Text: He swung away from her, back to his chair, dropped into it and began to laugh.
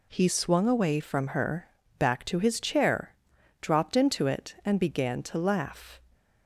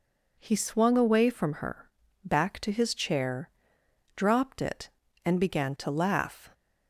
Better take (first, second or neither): first